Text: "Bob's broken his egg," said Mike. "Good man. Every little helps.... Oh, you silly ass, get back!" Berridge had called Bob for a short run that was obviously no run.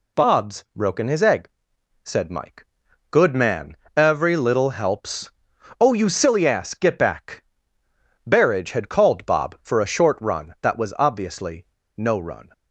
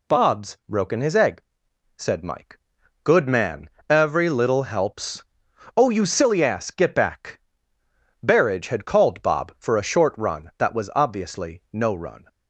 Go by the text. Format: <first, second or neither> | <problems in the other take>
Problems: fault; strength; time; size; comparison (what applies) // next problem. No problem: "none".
second | pauses between "obviously" and "no"; slight; at 11.6 s; 0.30 s long